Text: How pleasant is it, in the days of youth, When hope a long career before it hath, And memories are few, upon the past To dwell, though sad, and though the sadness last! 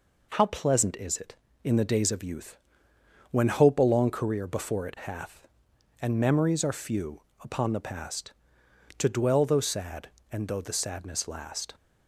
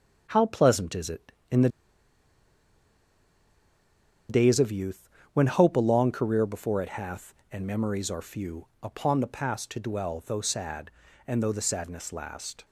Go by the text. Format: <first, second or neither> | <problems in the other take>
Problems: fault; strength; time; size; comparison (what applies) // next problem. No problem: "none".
first | starts louder than the rest; strong; until 1.3 s; 7 dB // pauses between "the" and "days"; strong; at 1.6 s; 2.6 s long